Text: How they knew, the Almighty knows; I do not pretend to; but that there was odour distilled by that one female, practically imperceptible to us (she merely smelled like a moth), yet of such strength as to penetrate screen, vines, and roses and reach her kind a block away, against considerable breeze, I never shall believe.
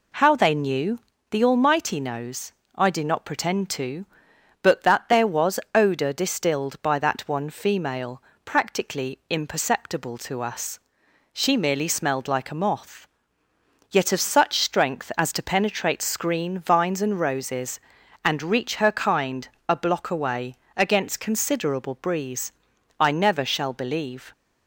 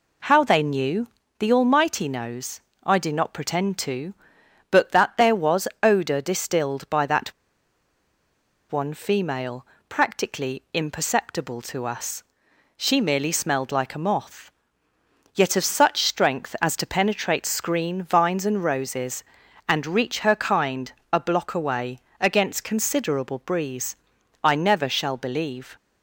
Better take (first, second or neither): first